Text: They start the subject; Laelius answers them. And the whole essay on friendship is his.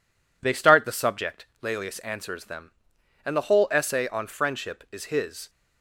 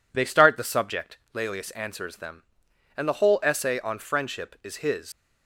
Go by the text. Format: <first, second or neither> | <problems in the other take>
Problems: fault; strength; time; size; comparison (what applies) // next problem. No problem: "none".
first | leaves "his" unfinished; at 5.1 s; 90 ms